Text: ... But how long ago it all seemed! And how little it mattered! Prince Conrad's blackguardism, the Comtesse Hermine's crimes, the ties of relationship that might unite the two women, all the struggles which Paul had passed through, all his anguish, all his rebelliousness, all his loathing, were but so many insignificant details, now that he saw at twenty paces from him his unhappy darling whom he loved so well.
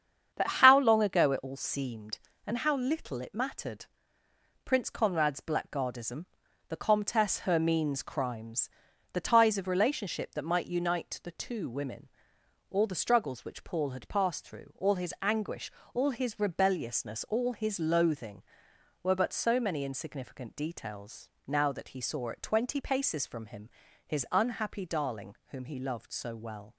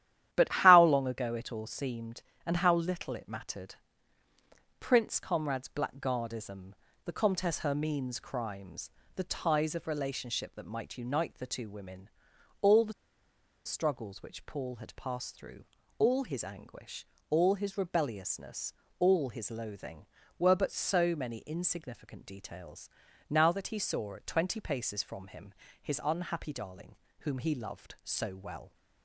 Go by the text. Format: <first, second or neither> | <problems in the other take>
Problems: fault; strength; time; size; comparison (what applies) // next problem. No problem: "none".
first | starts louder than the rest; strong; until 1.3 s; 11.5 dB; strong in the first // pauses between "the" and "struggles"; noticeable; at 12.9 s; 0.72 s long // pauses between "him" and "his"; slight; at 25.5 s; 0.28 s long; also in the first // pauses between "darling" and "whom"; slight; at 26.9 s; 0.24 s long